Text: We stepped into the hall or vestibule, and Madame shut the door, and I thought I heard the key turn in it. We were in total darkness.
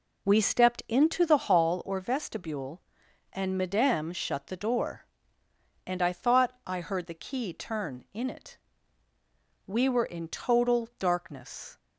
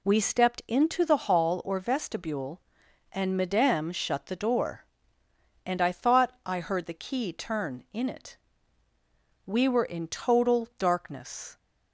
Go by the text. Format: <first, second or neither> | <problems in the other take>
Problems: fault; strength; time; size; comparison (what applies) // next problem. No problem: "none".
second | starts louder than the rest; until 1.8 s; 3.5 dB